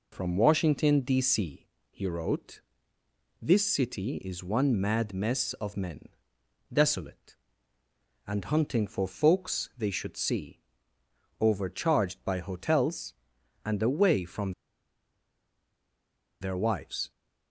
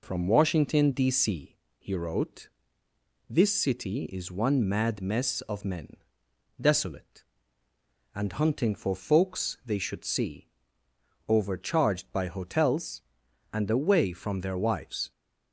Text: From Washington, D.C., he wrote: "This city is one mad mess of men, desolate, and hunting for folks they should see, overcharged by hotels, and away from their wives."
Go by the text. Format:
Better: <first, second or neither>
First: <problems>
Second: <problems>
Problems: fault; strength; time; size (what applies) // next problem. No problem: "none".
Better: second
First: pauses between "from" and "their"; strong; at 14.5 s; 1.9 s long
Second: none